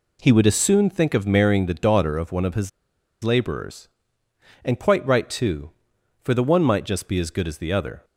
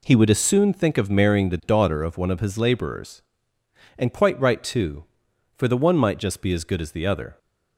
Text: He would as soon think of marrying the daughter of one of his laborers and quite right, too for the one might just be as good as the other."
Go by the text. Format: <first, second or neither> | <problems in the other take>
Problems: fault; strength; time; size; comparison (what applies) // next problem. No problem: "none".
second | pauses between "his" and "laborers"; noticeable; at 2.6 s; 0.54 s long